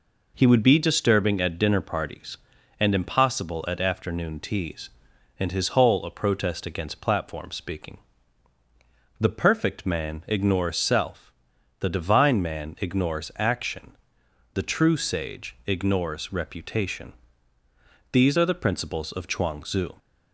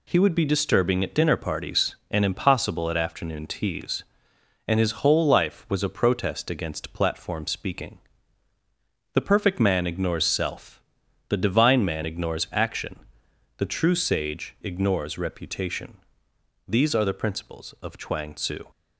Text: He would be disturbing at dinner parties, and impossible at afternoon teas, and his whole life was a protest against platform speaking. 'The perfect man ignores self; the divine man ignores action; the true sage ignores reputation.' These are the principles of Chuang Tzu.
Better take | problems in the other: second | skips "life was"; at 6.0 s

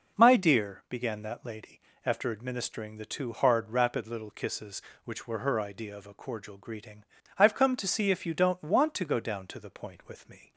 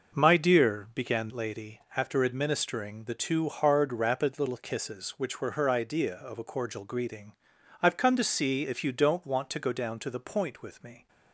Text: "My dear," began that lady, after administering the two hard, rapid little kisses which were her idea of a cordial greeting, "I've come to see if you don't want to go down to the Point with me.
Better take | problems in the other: first | skips "that"; at 1.3 s

